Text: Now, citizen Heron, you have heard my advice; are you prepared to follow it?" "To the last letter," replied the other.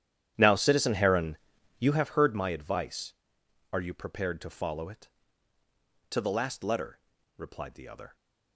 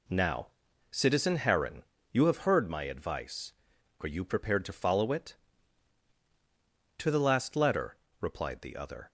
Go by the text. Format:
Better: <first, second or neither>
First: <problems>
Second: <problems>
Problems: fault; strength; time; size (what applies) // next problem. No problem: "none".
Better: second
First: starts louder than the rest; strong; until 2.0 s; 10.5 dB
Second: none